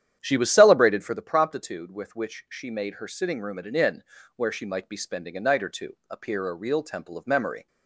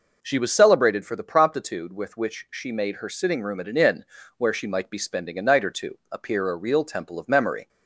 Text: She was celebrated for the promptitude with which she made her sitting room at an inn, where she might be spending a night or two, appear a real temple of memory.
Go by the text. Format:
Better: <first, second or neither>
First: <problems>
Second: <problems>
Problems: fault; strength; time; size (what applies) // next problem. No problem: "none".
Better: second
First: starts louder than the rest; strong; until 1.2 s; 10 dB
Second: none